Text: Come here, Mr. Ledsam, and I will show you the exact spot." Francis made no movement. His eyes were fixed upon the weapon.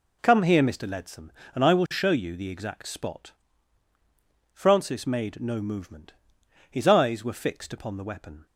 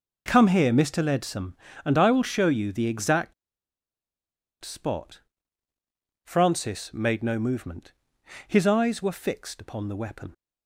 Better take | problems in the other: first | pauses between "exact" and "spot"; strong; at 3.3 s; 1.2 s long

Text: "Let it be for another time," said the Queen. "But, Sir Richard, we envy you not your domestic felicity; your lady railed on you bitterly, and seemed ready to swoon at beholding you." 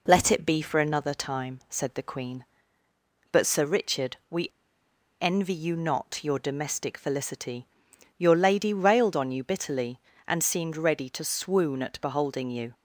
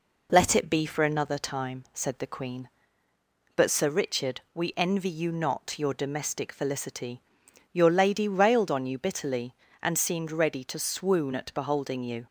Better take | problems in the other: second | pauses between "we" and "envy"; noticeable; at 4.4 s; 0.72 s long

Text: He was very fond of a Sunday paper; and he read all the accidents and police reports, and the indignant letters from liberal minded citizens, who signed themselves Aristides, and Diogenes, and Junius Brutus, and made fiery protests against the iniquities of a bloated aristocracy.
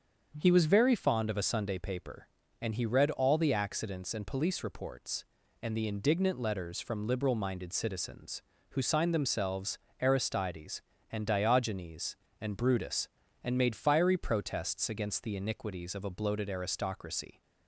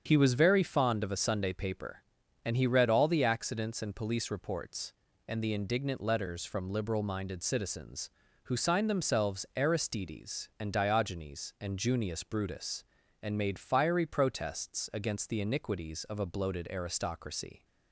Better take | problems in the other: second | starts louder than the rest; until 1.3 s; 7 dB; strong in the second // pauses between "themselves" and "Aristides"; slight; at 9.7 s; 0.22 s long // skips "Junius"; at 12.5 s

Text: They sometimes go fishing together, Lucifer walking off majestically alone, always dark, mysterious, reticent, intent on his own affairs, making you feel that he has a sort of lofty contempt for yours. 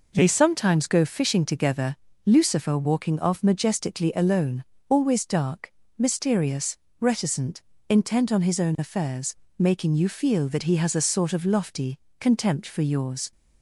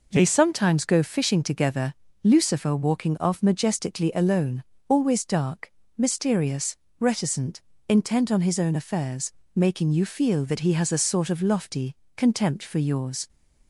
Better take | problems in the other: neither | pauses between "lofty" and "contempt"; slight; the same in both

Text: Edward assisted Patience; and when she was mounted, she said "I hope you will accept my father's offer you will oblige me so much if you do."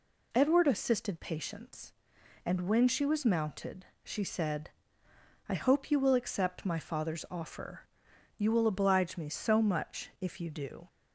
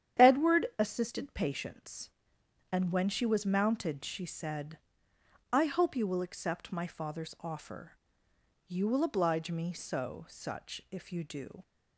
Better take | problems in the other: first | starts louder than the rest; strong; until 1.3 s; 9.5 dB // pauses between "said" and "I"; noticeable; at 4.7 s; 0.74 s long; noticeable in the first // pauses between "offer" and "you"; noticeable; at 7.9 s; 0.74 s long; noticeable in the first // says "such" for "much"; at 10.2 s

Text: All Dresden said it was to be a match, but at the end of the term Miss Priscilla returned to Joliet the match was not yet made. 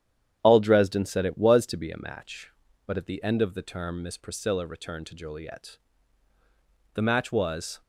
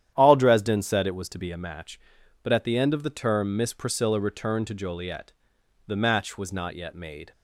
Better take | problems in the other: second | starts louder than the rest; strong; until 1.4 s; 9.5 dB; strong in the second // pauses between "Joliet" and "the"; at 5.7 s; 1.1 s long; noticeable in the second // stops before "not yet made"; at 7.8 s

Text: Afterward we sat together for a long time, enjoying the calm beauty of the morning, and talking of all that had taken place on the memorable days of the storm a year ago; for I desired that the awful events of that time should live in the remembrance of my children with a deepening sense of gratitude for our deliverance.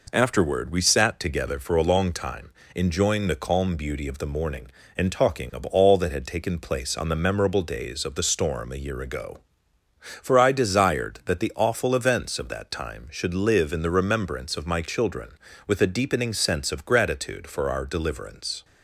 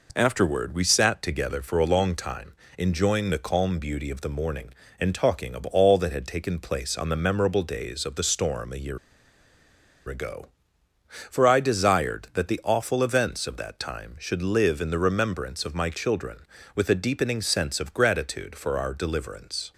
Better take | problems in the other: first | pauses between "year" and "ago"; at 8.9 s; 1.1 s long

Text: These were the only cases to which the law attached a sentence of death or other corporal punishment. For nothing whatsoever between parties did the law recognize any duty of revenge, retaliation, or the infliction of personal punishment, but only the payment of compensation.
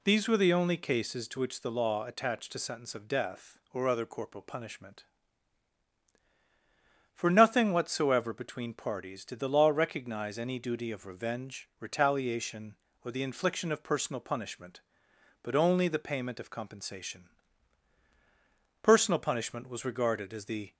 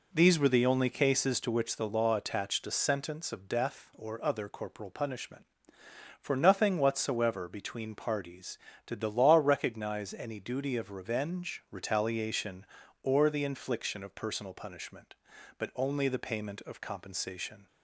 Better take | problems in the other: second | goes on to say "Personal punishment was regarded as the"; strong; from 18.8 s on; 1.9 s long

